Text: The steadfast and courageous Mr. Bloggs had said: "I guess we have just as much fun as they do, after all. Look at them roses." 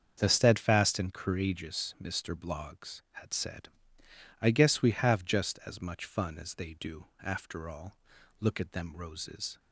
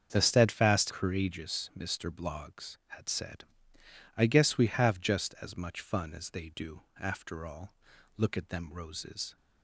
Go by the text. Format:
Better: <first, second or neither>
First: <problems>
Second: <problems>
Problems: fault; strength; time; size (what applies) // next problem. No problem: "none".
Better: first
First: starts louder than the rest; until 1.1 s; 7 dB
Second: starts louder than the rest; until 1.1 s; 7 dB // skips "and"; at 0.9 s